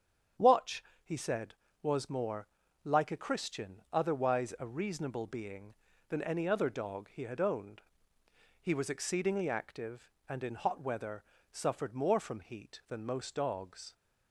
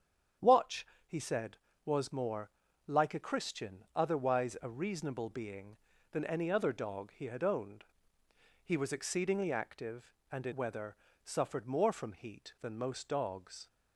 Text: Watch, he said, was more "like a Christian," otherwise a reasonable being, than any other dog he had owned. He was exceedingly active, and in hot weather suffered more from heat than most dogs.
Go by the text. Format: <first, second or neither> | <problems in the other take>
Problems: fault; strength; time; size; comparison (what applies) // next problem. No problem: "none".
first | starts louder than the rest; strong; until 1.8 s; 8 dB; strong in the first // pauses between "more" and "like"; slight; at 2.4 s; 0.36 s long; slight in the first // skips "hot"; at 10.5 s // pauses between "weather" and "suffered"; slight; at 10.9 s; 0.28 s long; slight in the first